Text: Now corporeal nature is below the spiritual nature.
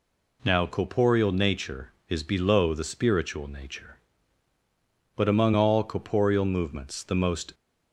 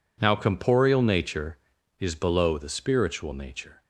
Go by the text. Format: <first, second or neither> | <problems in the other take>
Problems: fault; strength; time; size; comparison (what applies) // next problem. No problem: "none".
second | goes on to say "But among all corporeal movements the most"; strong; from 5.1 s on; 2.3 s long